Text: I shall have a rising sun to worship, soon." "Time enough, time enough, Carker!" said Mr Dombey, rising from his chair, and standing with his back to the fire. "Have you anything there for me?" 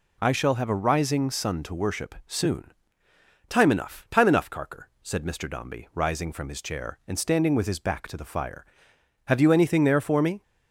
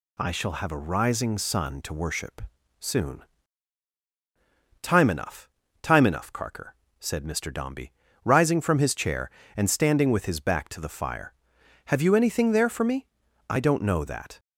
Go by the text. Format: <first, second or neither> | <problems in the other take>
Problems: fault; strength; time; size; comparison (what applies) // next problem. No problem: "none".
first | goes on to say "I don't know that"; noticeable; from 13.4 s on; 0.90 s long